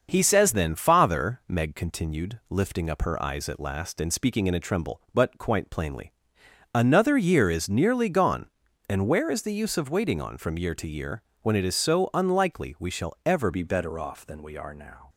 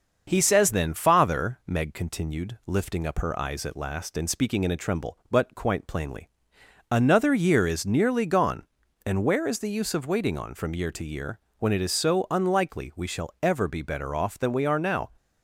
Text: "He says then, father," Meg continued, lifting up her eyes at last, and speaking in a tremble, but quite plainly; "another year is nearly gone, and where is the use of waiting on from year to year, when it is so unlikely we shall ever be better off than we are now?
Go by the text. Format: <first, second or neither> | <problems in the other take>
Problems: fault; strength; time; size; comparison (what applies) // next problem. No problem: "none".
second | starts louder than the rest; until 1.1 s; 6.5 dB; also in the second // changes voice at "be"; from 13.5 s on; 1.5 s long